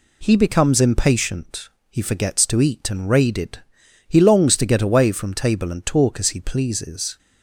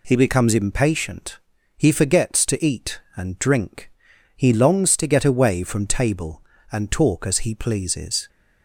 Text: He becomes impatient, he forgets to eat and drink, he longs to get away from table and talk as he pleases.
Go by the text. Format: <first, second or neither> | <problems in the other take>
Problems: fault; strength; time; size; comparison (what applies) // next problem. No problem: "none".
second | says "raided" for "drink"; at 3.0 s